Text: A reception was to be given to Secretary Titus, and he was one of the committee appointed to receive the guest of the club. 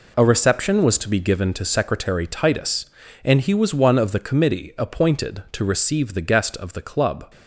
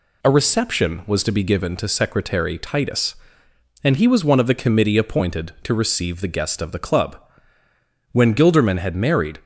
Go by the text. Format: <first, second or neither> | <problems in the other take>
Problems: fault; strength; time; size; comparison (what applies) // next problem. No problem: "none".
first | goes on to say "When Gilderman had married"; noticeable; from 8.1 s on; 1.2 s long